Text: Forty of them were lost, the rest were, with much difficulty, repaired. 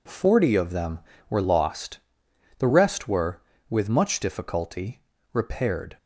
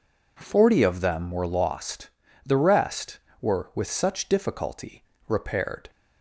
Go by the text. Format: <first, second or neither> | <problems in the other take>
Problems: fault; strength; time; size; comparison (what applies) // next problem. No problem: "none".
first | says "such" for "much"; at 3.9 s